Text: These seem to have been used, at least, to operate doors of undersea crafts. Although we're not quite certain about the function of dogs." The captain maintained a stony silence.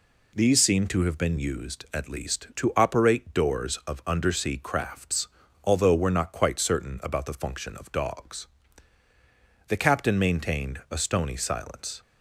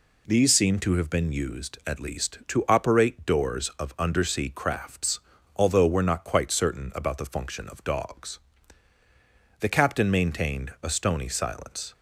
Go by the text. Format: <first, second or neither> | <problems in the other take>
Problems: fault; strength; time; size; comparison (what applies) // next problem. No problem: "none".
neither | none